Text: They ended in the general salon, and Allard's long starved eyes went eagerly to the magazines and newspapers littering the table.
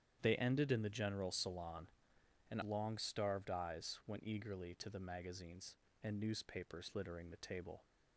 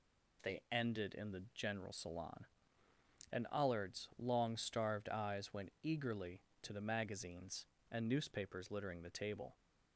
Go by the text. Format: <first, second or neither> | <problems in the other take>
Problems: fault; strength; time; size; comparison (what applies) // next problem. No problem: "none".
second | starts louder than the rest; strong; until 1.2 s; 9.5 dB // skips "Allard's"; at 2.6 s